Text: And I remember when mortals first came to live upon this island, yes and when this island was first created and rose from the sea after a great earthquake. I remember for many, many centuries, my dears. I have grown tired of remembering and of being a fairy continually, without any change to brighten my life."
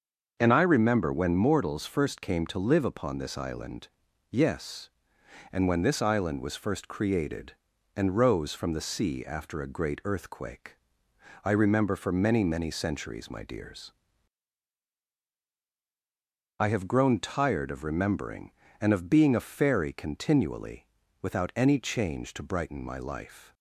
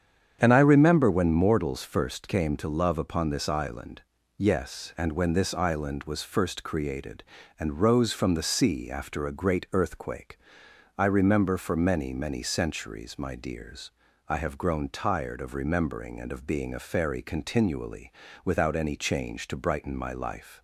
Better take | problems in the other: first | starts louder than the rest; strong; until 1.4 s; 8 dB; also in the first // says "love" for "live"; at 2.6 s

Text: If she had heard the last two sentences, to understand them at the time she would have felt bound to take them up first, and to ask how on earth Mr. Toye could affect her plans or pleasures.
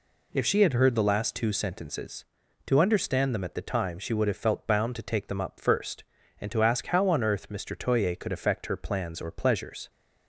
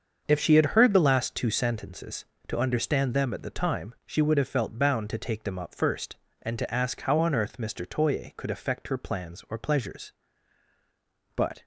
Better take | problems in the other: first | starts louder than the rest; until 1.2 s; 6.5 dB // goes on to say "But"; slight; from 11.3 s on; 0.30 s long

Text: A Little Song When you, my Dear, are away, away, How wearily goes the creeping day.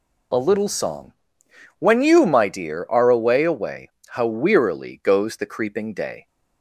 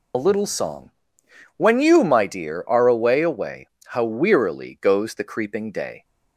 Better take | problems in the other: first | loses the start of "A"; at 0.1 s; 55 ms // pauses between "Song" and "When"; noticeable; at 0.9 s; 0.66 s long; noticeable in the first

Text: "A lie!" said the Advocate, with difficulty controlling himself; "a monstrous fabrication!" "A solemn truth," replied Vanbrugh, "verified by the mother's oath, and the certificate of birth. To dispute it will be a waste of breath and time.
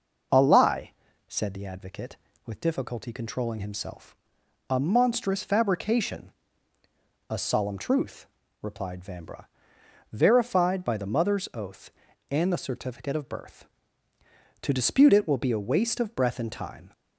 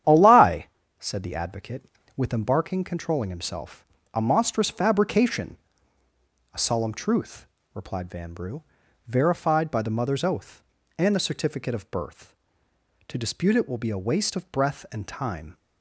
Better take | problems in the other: first | starts louder than the rest; strong; until 1.4 s; 10 dB // says "embarking" for "difficulty"; at 2.3 s

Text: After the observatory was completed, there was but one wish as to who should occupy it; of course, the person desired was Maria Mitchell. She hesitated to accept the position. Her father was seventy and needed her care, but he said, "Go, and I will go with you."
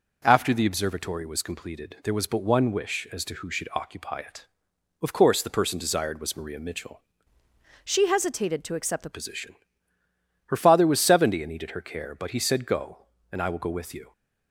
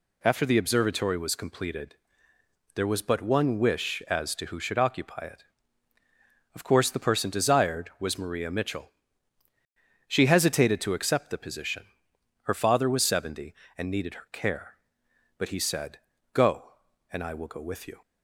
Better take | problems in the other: second | changes voice from "She" to "the"; from 7.8 to 9.0 s; 1.2 s long

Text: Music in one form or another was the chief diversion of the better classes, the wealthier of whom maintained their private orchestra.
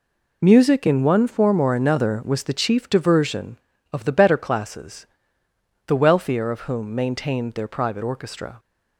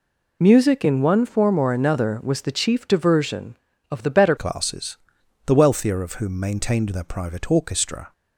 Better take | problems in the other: first | changes voice at "classes"; from 4.3 s on; 3.8 s long

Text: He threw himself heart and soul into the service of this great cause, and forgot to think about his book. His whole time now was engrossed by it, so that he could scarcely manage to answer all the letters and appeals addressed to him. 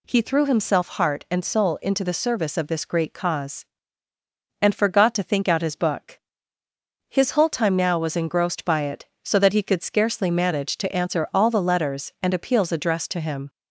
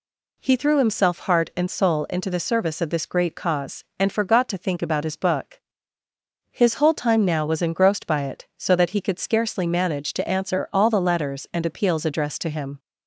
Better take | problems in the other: second | says "out" for "about"; at 5.4 s

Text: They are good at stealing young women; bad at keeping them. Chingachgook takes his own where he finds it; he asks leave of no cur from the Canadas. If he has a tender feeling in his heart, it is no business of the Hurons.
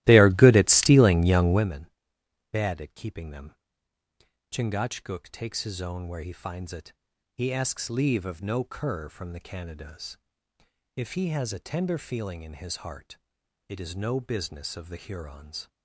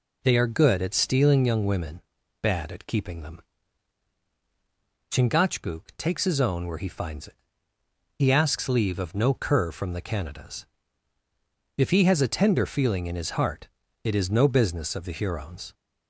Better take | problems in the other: second | starts louder than the rest; strong; until 1.7 s; 16 dB

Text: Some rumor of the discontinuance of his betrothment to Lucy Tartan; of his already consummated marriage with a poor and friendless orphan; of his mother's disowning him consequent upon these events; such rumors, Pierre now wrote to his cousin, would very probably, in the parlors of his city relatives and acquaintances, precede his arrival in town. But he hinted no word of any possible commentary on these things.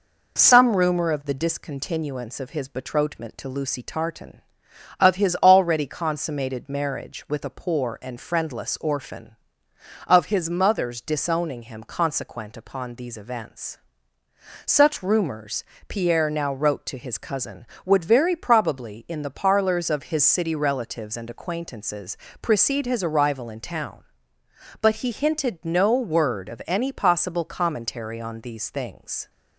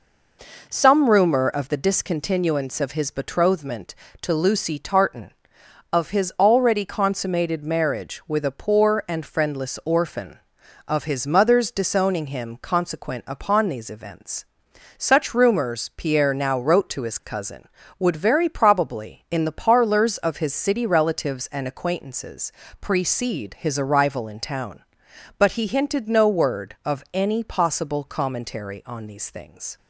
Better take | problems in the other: neither | none

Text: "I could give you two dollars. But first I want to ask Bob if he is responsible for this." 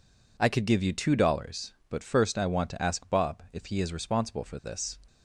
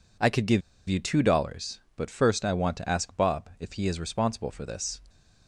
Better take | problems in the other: first | pauses between "give" and "you"; slight; at 0.6 s; 0.26 s long

